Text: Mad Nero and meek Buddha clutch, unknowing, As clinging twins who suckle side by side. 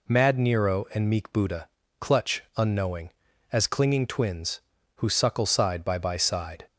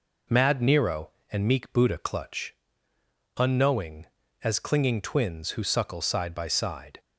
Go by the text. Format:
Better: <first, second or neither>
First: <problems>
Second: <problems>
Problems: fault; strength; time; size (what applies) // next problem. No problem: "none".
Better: second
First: pauses between "Buddha" and "clutch"; slight; at 1.6 s; 0.30 s long // says "by" twice; at 5.9 s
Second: none